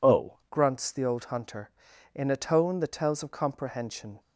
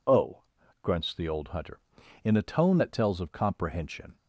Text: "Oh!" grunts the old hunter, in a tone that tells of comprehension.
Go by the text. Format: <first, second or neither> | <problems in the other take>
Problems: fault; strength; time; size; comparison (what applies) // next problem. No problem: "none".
second | changes voice at "grunts"; from 0.4 s on; 3.7 s long